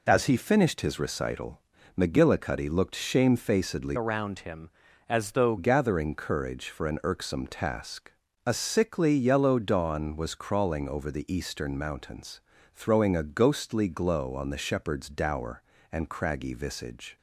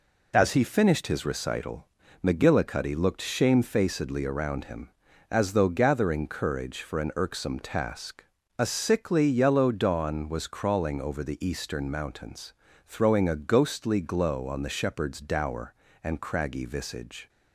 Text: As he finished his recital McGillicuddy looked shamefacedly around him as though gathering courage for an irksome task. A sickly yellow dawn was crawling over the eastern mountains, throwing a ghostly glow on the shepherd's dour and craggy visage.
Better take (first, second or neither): second